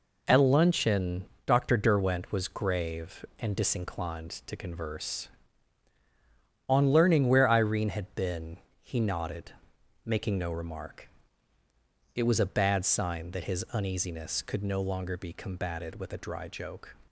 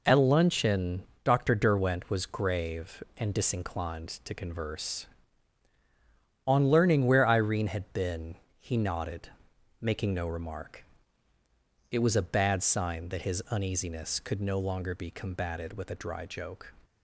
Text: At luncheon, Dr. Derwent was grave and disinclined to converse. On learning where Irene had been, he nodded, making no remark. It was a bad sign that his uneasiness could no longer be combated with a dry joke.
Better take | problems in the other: neither | none

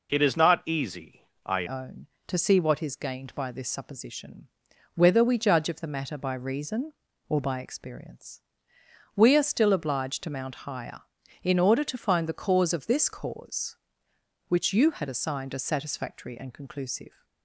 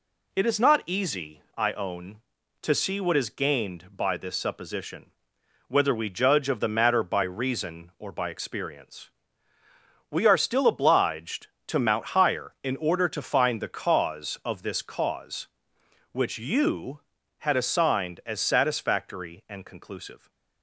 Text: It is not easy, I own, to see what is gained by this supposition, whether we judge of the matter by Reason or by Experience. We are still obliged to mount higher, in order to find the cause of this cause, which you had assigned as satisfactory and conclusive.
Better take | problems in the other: second | changes voice at "own"; from 1.6 s on; 15.6 s long

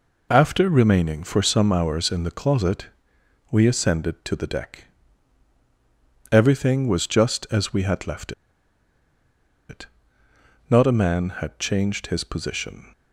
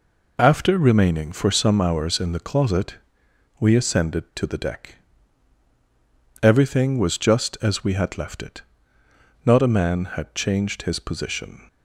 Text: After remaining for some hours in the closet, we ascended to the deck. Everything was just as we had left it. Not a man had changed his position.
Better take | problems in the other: second | pauses between "left" and "it"; strong; at 8.3 s; 1.3 s long

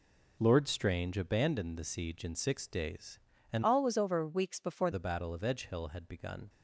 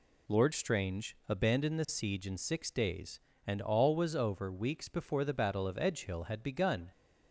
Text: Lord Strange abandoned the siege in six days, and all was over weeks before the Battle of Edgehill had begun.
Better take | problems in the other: second | changes voice from "all" to "before"; from 3.6 to 4.9 s; 1.3 s long

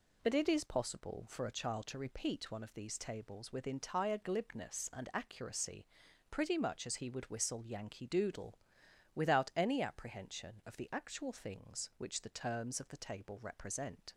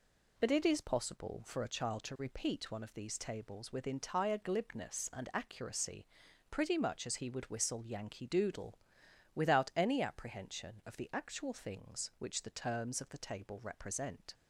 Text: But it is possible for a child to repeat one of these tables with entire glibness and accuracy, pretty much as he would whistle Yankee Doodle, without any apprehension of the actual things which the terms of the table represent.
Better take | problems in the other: neither | none

